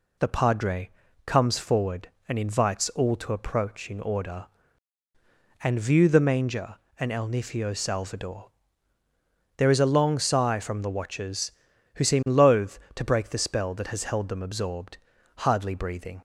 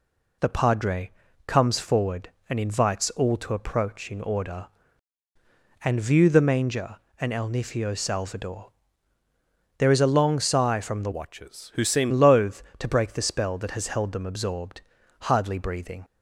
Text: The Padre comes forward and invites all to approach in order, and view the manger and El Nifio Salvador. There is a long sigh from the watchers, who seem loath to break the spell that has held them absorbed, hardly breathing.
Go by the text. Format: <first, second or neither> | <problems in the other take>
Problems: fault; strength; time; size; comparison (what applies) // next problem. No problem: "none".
first | pauses between "Padre" and "comes"; slight; at 1.1 s; 0.36 s long; slight in the first // changes voice from "watchers" to "seem"; from 11.1 to 12.1 s; 1.0 s long